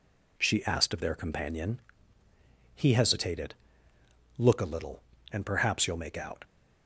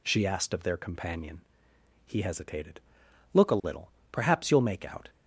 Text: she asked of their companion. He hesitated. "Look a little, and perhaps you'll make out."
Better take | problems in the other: first | skips "and"; at 4.0 s

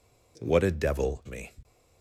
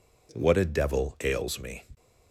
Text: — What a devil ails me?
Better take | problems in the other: second | skips "ails"; at 1.2 s

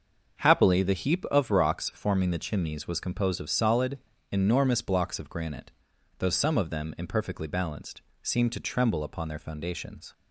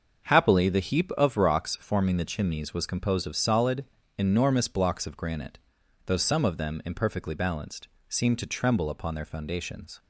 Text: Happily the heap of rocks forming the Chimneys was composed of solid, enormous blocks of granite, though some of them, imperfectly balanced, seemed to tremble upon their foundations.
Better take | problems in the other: neither | starts louder than the rest; the same in both

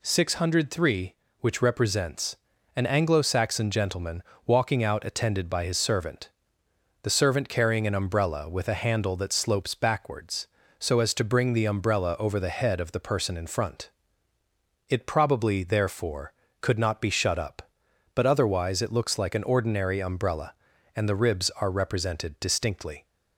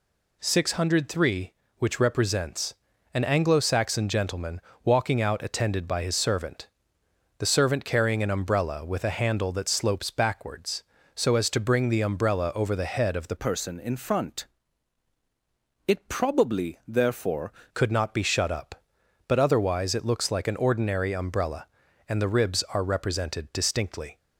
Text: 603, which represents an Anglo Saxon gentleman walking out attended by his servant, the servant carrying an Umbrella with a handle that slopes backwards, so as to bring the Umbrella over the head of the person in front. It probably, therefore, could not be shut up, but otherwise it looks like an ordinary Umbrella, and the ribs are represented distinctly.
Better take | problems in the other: first | pauses between "represents" and "an"; at 2.7 s; 0.38 s long; also in the first // pauses between "gentleman" and "walking"; slight; at 4.6 s; 0.24 s long; slight in the first // changes voice from "person" to "therefore"; from 13.3 to 17.5 s; 4.2 s long

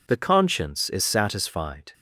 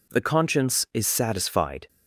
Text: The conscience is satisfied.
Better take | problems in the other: neither | none

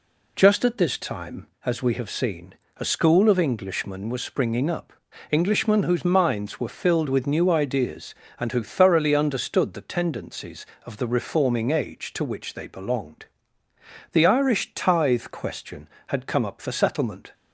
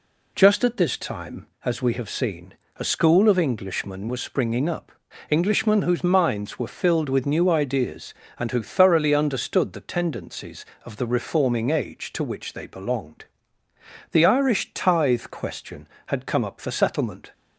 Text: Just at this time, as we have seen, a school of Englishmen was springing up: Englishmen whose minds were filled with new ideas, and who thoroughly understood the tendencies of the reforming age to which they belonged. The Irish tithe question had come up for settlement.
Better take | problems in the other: neither | none

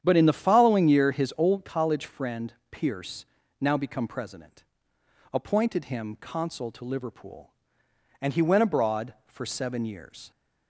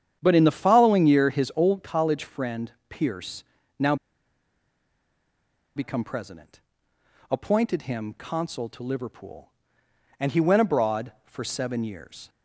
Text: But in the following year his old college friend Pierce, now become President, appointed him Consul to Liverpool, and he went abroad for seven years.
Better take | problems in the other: first | starts louder than the rest; strong; until 1.2 s; 9 dB; strong in the first // pauses between "friend" and "Pierce"; slight; at 2.7 s; 0.18 s long; slight in the first // pauses between "now" and "become"; strong; at 3.9 s; 1.8 s long

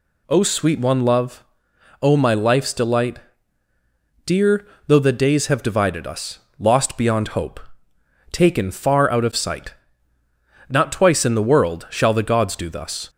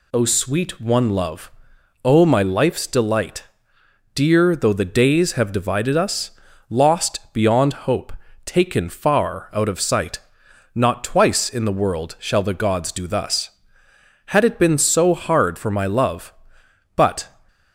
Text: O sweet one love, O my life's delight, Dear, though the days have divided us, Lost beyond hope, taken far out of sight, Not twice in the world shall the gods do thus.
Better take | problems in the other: first | goes on to say "Had it been so hard for my love but"; strong; from 14.2 s on; 3.0 s long

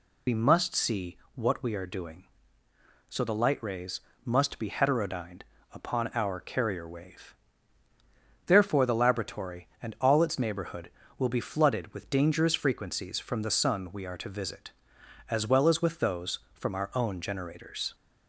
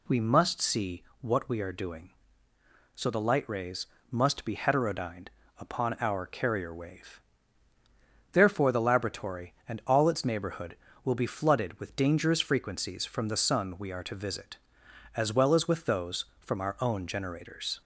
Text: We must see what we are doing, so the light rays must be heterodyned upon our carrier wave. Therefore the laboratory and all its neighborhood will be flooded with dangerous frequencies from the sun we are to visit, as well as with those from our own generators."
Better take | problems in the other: second | loses the start of "We"; at 0.2 s; 65 ms // pauses between "see" and "what"; slight; at 1.1 s; 0.18 s long; slight in the second // pauses between "rays" and "must"; slight; at 4.0 s; 0.22 s long; slight in the second // pauses between "heterodyned" and "upon"; slight; at 5.4 s; 0.32 s long; slight in the second

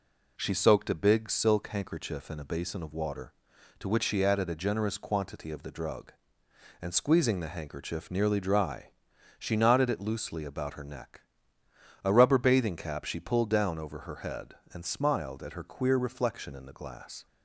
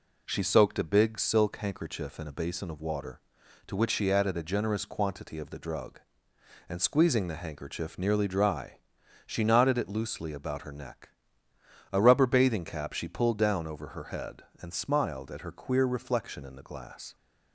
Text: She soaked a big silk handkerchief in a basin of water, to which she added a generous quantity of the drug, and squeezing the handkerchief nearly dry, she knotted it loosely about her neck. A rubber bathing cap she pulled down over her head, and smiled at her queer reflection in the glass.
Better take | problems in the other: neither | none

